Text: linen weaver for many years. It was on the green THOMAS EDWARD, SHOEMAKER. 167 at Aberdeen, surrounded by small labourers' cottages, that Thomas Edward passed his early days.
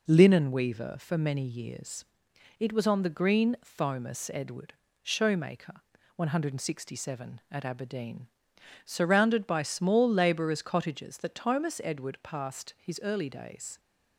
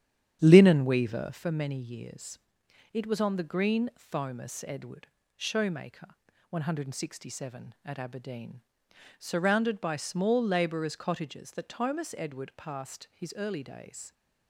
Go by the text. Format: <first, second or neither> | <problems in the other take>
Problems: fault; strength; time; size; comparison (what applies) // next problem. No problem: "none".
first | starts louder than the rest; strong; until 1.5 s; 9.5 dB